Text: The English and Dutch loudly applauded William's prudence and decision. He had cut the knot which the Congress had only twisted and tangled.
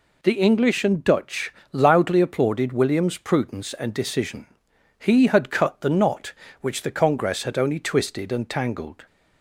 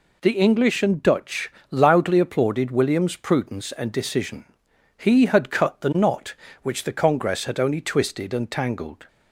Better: neither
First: pauses between "Dutch" and "loudly"; slight; at 1.5 s; 0.18 s long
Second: pauses between "Dutch" and "loudly"; slight; at 1.5 s; 0.18 s long

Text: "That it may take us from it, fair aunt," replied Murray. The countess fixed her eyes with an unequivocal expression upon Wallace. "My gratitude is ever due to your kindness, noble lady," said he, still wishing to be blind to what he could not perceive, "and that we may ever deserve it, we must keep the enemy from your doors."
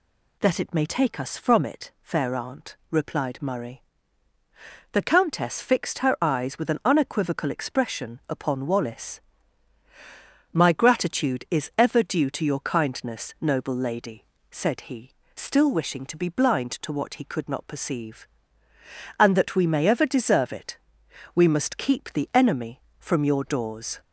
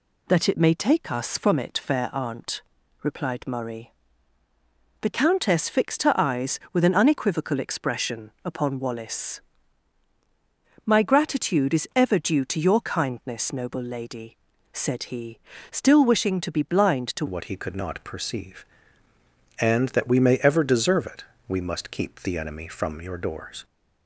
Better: first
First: none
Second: changes voice at "what"; from 17.2 s on; 6.4 s long

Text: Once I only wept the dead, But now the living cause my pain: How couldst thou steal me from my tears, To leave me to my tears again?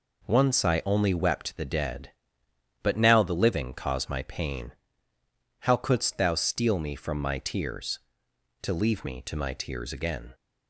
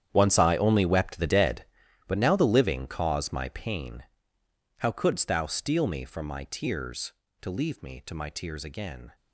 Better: first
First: none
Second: gets quieter; strong; throughout; 13.5 dB

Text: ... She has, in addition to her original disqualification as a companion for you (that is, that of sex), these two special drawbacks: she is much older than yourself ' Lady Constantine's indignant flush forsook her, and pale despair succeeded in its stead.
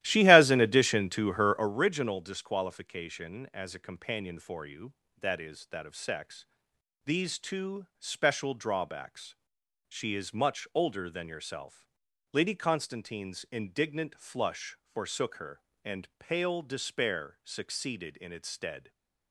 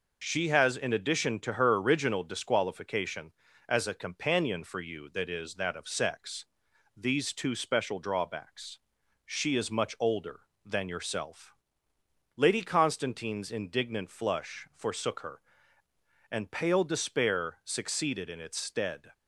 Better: second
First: starts louder than the rest; strong; until 1.8 s; 14.5 dB // pauses between "flush" and "forsook"; slight; at 14.7 s; 0.16 s long // stays silent after the last word; slight; from 18.7 s on; 0.6 s long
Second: none

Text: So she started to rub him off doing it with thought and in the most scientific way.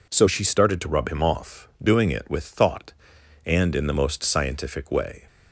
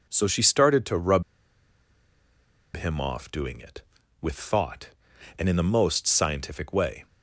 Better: first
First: none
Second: pauses between "rub" and "him"; strong; at 1.2 s; 1.5 s long

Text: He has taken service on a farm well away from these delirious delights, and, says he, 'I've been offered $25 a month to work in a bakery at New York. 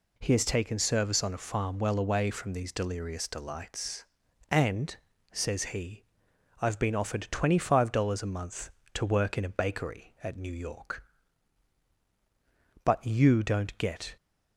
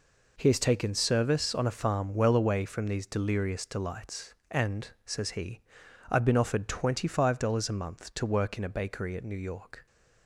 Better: second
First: goes on to say "But you don't get"; from 12.8 s on; 1.3 s long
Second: none

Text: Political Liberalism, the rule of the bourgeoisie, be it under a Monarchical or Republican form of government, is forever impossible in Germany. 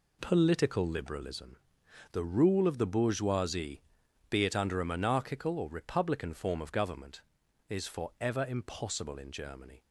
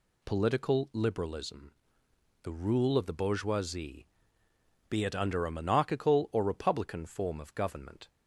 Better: first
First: none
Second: stops before "is forever impossible in Germany"; at 8.0 s

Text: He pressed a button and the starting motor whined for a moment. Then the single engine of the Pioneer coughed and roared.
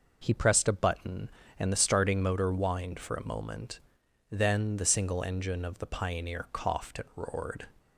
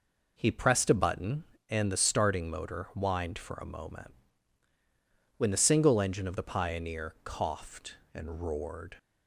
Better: first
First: none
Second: says "When" for "Then"; at 5.3 s

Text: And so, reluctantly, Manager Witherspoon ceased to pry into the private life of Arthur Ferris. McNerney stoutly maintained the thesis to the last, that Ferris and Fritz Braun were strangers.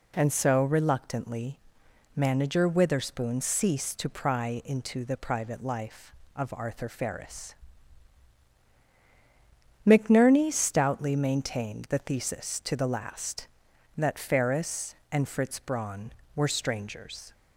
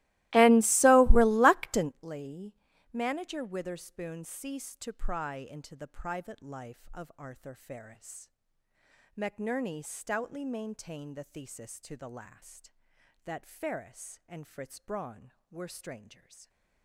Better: first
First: none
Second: starts louder than the rest; strong; until 1.9 s; 18.5 dB // stays silent after the last word; slight; from 15.9 s on; 0.9 s long

